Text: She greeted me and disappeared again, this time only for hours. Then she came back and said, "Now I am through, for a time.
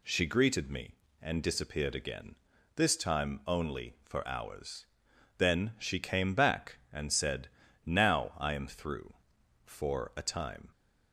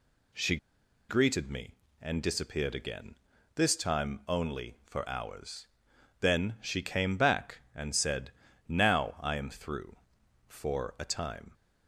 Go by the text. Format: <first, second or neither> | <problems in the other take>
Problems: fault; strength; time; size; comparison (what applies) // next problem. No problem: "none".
first | pauses between "She" and "greeted"; noticeable; at 0.5 s; 0.52 s long